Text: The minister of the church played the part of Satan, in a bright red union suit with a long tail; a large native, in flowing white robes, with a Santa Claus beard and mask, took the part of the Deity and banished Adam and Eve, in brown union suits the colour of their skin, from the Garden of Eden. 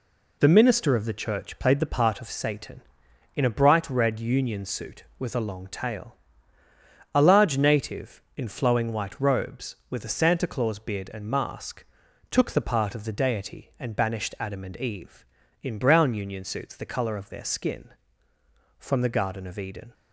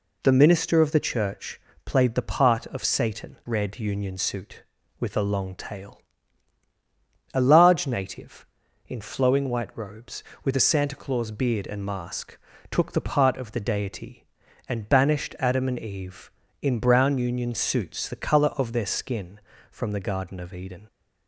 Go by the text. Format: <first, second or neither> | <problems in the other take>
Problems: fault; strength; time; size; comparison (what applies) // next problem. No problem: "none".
first | pauses between "church" and "played"; slight; at 1.6 s; 0.24 s long // skips "in a bright"; at 3.4 s